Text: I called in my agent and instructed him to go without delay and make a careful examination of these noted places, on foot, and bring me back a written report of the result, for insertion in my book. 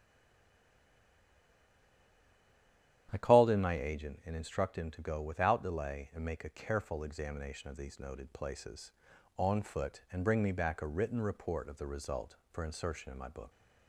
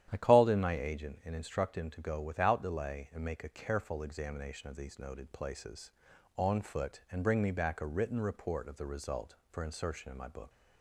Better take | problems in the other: second | stays silent before the first word; strong; until 3.0 s; 3.0 s long // starts louder than the rest; strong; until 4.1 s; 11 dB; strong in the second

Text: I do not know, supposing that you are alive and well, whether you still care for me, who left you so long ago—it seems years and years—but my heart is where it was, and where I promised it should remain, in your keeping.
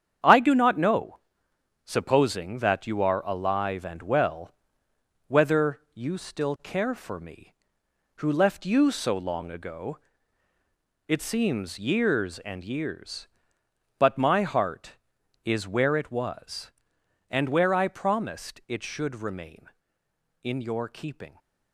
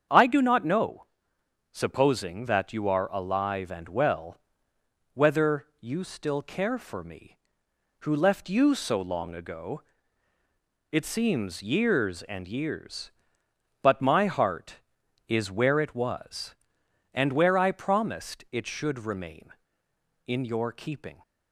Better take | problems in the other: second | gets quieter; strong; throughout; 7.5 dB // starts louder than the rest; strong; until 1.9 s; 8.5 dB; strong in the second // pauses between "whether" and "you"; slight; at 5.7 s; 0.16 s long; slight in the second

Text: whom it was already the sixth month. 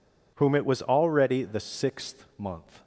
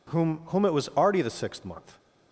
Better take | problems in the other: first | says "whom" twice; at 0.4 s

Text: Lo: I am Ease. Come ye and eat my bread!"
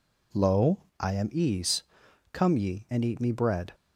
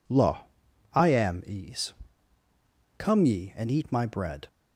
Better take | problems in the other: second | says "me" for "my"; at 3.1 s

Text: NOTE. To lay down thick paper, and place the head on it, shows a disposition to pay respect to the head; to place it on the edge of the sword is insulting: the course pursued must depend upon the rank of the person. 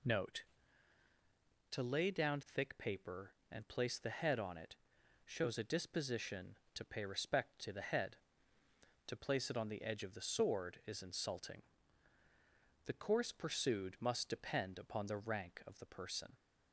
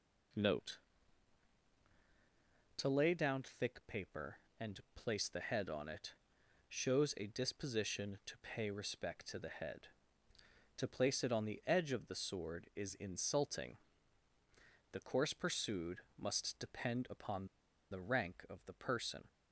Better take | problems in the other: first | pauses between "and" and "place"; slight; at 4.7 s; 0.16 s long // pauses between "pursued" and "must"; slight; at 15.9 s; 0.18 s long // pauses between "upon" and "the"; at 17.4 s; 0.43 s long

